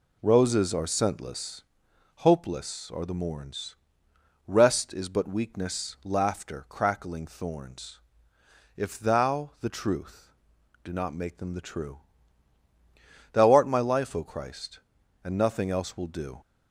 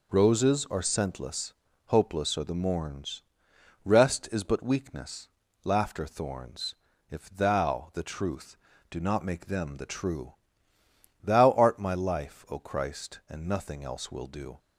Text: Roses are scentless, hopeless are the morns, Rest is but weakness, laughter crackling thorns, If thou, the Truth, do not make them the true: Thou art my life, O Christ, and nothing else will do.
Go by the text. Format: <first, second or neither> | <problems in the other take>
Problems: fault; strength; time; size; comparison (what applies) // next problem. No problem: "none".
first | skips "crackling"; at 6.0 s